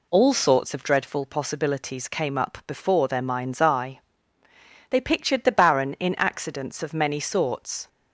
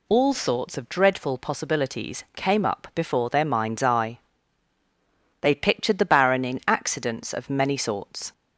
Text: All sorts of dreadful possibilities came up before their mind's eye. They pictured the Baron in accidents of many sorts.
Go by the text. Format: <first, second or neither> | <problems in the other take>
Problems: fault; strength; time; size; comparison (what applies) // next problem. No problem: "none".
neither | none